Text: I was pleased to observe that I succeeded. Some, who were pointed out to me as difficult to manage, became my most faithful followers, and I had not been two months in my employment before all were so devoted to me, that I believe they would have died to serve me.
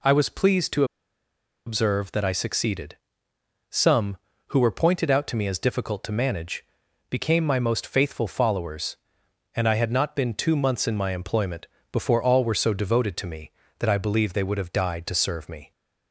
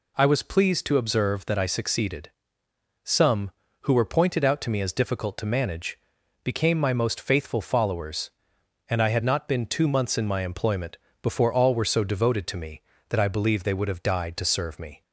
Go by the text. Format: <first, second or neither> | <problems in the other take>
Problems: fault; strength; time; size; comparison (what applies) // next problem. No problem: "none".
second | pauses between "to" and "observe"; noticeable; at 0.8 s; 0.82 s long // pauses between "employment" and "before"; slight; at 11.6 s; 0.26 s long; slight in the second